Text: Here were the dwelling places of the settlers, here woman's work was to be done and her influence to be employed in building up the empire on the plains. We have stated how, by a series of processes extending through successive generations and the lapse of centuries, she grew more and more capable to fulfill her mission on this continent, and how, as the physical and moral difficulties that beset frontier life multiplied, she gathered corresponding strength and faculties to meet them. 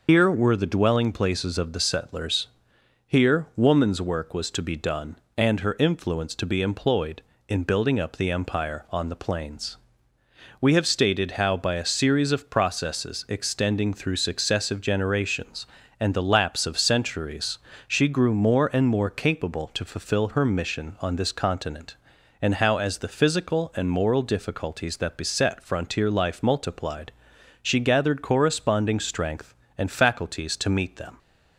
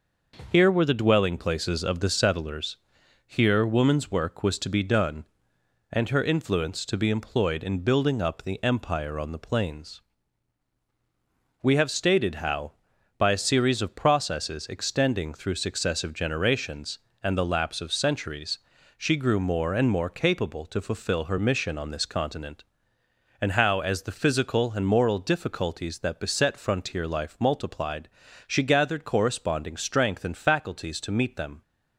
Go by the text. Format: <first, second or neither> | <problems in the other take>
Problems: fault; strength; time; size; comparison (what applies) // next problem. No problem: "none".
second | loses the start of "Here"; at 0.0 s; 95 ms